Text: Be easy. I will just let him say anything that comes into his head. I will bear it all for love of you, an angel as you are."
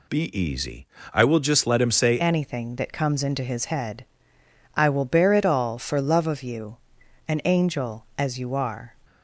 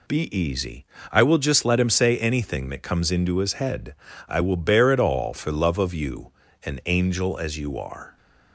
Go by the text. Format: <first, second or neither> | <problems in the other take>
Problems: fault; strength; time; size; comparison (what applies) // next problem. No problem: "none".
second | changes voice at "anything"; from 2.1 s on; 6.8 s long